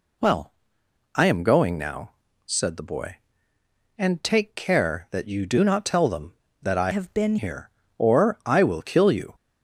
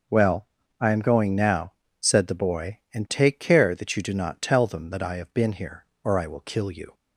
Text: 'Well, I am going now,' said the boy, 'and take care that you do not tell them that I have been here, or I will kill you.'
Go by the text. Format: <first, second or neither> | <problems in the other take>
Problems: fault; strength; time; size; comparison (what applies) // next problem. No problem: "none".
second | changes voice from "have" to "been"; from 6.9 to 7.3 s; 0.4 s long